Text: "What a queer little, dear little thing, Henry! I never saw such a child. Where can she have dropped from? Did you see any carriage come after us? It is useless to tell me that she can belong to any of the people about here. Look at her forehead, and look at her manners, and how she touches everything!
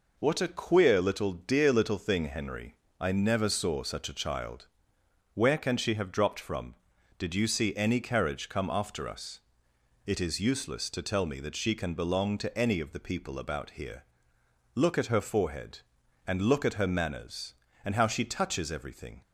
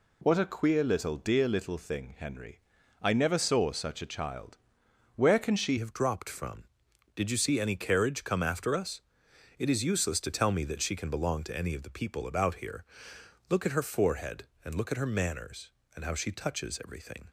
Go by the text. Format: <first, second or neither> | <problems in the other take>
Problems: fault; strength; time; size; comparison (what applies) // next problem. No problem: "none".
first | changes voice at "have"; from 5.7 s on; 11.5 s long